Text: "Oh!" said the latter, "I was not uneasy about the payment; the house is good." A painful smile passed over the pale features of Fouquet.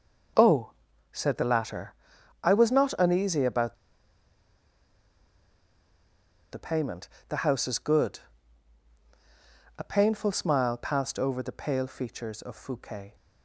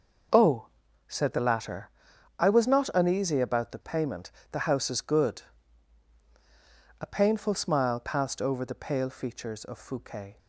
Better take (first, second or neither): second